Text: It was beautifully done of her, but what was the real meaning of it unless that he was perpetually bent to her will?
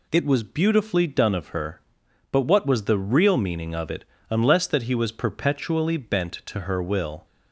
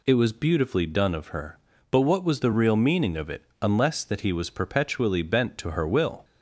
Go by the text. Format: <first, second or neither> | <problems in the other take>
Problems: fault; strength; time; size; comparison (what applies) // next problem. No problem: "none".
neither | pauses between "it" and "unless"; slight; the same in both